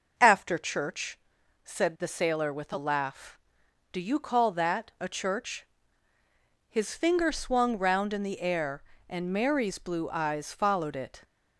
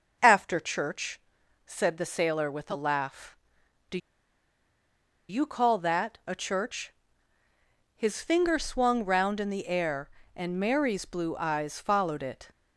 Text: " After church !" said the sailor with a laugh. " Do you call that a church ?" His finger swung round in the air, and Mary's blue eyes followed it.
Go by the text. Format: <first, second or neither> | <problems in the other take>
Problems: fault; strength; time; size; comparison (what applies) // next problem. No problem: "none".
first | starts louder than the rest; until 1.4 s; 6 dB; also in the first // pauses between "Do" and "you"; strong; at 3.9 s; 1.3 s long